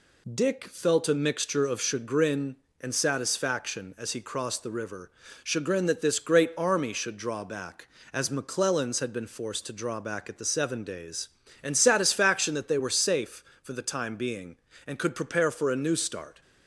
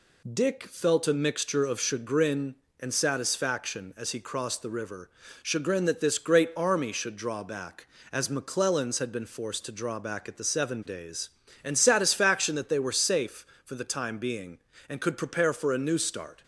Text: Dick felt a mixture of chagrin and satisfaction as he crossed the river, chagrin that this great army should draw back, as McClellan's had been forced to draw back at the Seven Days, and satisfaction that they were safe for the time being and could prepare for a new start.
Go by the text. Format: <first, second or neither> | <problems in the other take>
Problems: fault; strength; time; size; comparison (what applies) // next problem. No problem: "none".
neither | none